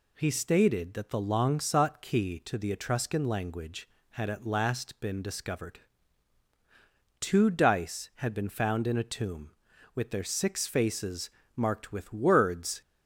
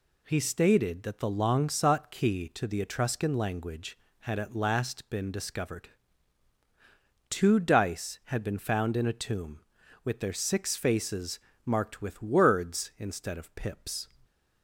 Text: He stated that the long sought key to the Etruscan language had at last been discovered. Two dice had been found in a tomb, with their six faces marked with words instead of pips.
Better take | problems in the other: second | pauses between "faces" and "marked"; slight; at 11.2 s; 0.28 s long; slight in the second // stops before "instead of pips"; at 12.8 s

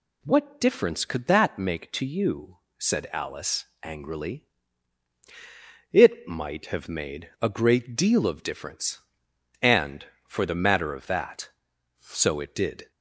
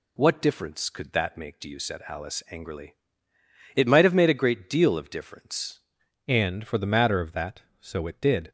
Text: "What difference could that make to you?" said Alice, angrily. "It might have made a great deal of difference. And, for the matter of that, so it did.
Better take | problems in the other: first | changes voice at "And"; from 6.2 s on; 2.3 s long

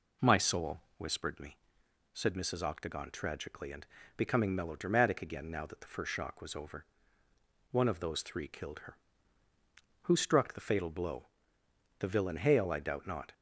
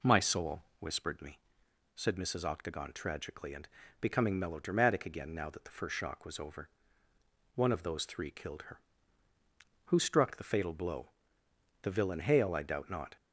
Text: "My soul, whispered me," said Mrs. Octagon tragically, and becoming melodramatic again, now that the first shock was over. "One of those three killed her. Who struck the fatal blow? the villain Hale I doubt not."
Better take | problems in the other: neither | pauses between "and" and "becoming"; slight; the same in both

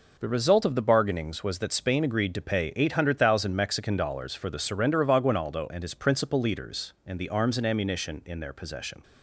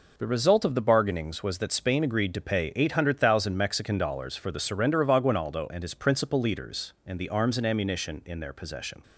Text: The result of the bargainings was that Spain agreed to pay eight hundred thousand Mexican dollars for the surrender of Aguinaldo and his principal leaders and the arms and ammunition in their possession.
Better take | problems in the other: neither | none

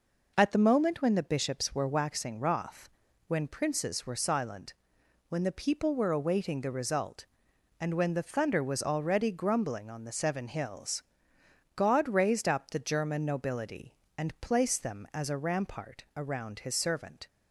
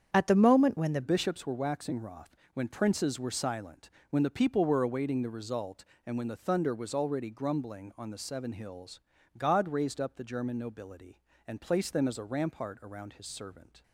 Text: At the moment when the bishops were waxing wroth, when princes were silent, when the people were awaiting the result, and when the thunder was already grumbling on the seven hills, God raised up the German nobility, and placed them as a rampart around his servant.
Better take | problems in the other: first | starts louder than the rest; strong; until 1.1 s; 8 dB // changes voice at "bishops"; from 1.0 s on; 12.8 s long

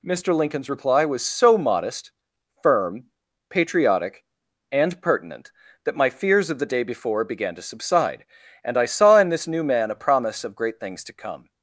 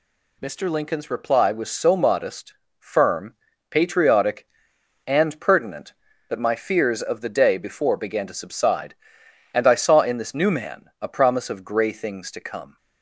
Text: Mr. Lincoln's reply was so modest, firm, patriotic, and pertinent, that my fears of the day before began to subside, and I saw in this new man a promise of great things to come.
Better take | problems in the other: first | says "grey" for "great"; at 11.6 s

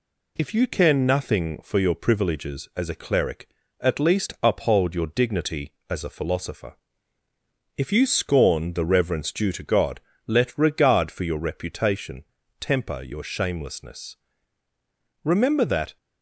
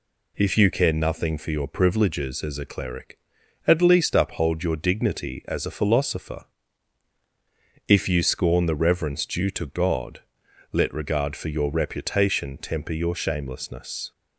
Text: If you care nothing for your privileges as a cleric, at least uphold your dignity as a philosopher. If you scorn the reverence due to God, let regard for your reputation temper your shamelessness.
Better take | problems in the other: second | pauses between "reputation" and "temper"; slight; at 12.2 s; 0.36 s long // goes on to say "Remember that"; noticeable; from 15.2 s on; 0.72 s long

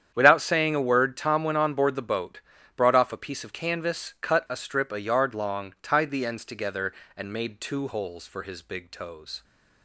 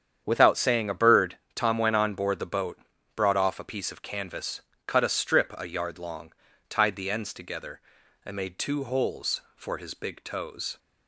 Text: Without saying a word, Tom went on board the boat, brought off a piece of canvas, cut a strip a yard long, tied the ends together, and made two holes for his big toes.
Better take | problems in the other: first | starts louder than the rest; strong; until 1.2 s; 8.5 dB; strong in the first // says "bird" for "word"; at 0.9 s

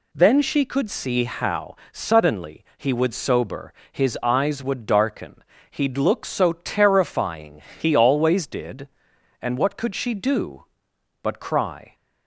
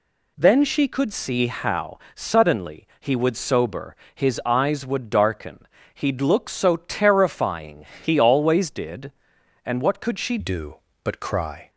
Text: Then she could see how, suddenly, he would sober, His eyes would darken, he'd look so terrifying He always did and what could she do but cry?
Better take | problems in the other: first | pauses between "terrifying" and "He"; slight; at 7.8 s; 0.16 s long; slight in the first // changes voice at "do"; from 10.3 s on; 1.3 s long

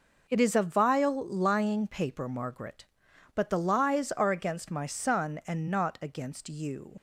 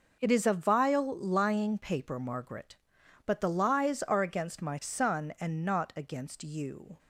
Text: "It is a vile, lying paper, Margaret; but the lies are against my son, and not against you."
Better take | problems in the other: second | leaves "you" unfinished; at 6.9 s; 60 ms

